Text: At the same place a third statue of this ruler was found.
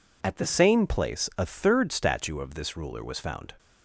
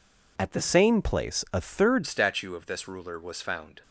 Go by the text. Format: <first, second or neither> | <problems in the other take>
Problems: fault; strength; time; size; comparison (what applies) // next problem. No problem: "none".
first | changes voice at "statue"; from 2.0 s on; 1.8 s long